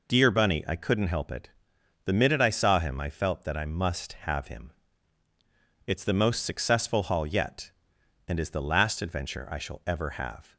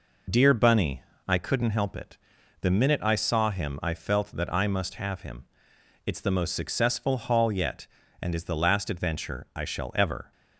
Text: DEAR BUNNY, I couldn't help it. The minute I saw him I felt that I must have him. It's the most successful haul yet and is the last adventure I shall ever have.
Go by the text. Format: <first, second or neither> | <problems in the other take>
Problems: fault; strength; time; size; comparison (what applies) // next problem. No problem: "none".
first | stops before "have"; at 10.3 s